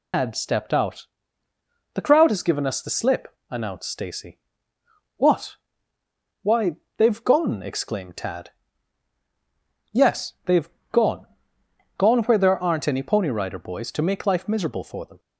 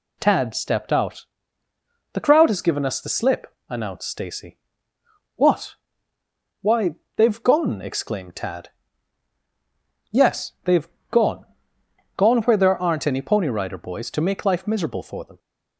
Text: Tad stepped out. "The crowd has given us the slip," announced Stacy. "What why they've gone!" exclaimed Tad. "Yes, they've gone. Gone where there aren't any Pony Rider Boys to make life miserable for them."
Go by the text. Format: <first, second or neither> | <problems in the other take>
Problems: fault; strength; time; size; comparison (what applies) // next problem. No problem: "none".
second | loses the start of "Tad"; at 0.1 s; 125 ms // pauses between "What" and "why"; noticeable; at 5.5 s; 0.84 s long; noticeable in the second // pauses between "why" and "they've"; slight; at 6.7 s; 0.18 s long; slight in the second // pauses between "they've" and "gone"; slight; at 10.6 s; 0.24 s long; slight in the second